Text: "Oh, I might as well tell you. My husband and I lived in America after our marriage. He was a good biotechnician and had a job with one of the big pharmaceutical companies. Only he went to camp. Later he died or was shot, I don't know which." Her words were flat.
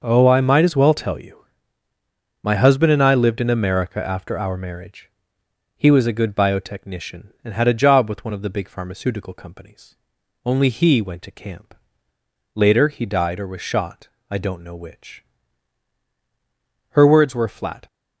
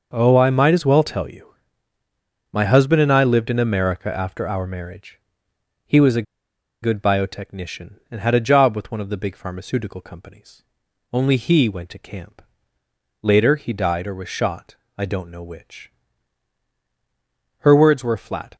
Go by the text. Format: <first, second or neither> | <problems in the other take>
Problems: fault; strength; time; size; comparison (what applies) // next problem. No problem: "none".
first | starts louder than the rest; noticeable; until 1.1 s; 6 dB; noticeable in the first // pauses between "a" and "good"; noticeable; at 6.2 s; 0.60 s long